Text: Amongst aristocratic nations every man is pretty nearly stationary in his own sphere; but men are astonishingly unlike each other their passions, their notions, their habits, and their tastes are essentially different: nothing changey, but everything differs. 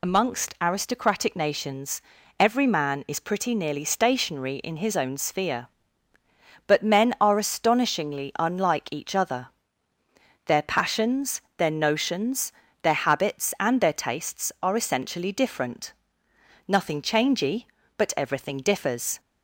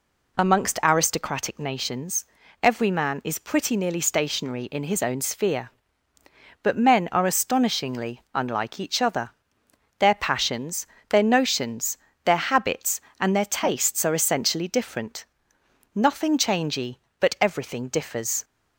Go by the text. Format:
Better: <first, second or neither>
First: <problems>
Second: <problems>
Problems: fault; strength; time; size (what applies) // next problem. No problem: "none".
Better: second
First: loses the start of "Amongst"; at 0.0 s; 95 ms // pauses between "nations" and "every"; at 2.0 s; 0.38 s long // pauses between "other" and "their"; noticeable; at 9.4 s; 0.96 s long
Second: pauses between "nations" and "every"; slight; at 2.2 s; 0.36 s long // pauses between "other" and "their"; noticeable; at 9.2 s; 0.70 s long